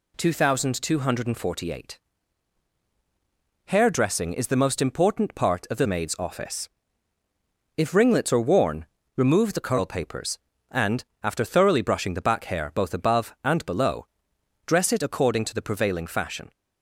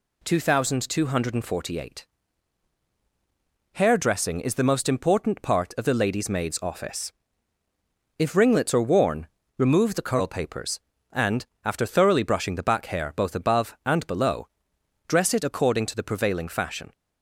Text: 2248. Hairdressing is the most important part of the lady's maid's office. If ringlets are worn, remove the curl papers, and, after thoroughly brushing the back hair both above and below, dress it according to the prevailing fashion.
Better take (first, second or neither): second